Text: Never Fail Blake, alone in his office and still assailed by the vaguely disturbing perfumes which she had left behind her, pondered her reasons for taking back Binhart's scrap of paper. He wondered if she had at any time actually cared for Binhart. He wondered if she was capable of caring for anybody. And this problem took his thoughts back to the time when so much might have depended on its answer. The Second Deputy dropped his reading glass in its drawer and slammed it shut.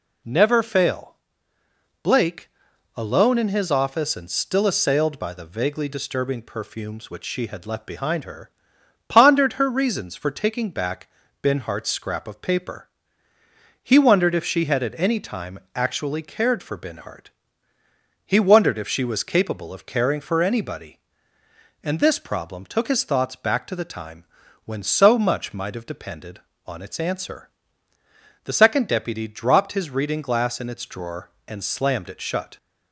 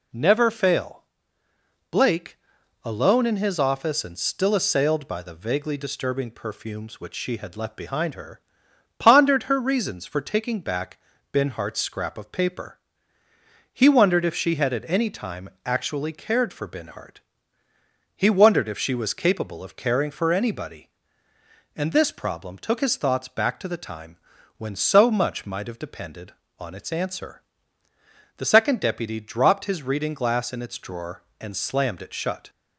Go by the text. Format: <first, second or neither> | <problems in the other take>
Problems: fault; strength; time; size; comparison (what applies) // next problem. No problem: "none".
neither | pauses between "Fail" and "Blake"; noticeable; the same in both // pauses between "back" and "Binhart's"; slight; the same in both // pauses between "time" and "actually"; slight; the same in both // pauses between "time" and "when"; the same in both